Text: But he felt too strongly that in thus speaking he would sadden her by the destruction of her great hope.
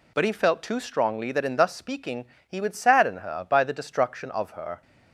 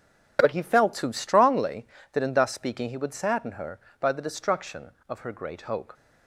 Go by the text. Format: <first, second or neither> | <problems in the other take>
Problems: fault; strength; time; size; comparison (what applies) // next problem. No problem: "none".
second | pauses between "speaking" and "he"; slight; at 2.2 s; 0.22 s long // stops before "great hope"; at 4.8 s